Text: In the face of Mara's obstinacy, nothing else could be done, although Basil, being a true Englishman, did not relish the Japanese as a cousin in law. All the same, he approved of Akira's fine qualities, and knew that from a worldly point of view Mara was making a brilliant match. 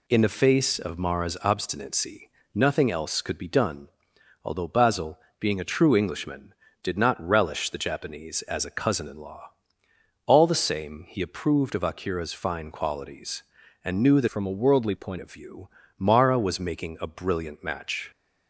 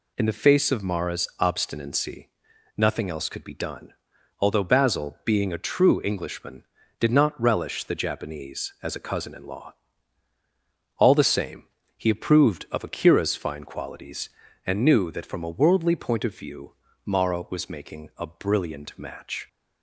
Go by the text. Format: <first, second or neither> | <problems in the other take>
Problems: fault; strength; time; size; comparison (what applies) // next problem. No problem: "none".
second | changes voice from "from" to "point"; from 14.2 to 15.1 s; 0.9 s long // pauses between "view" and "Mara"; slight; at 15.6 s; 0.28 s long; slight in the second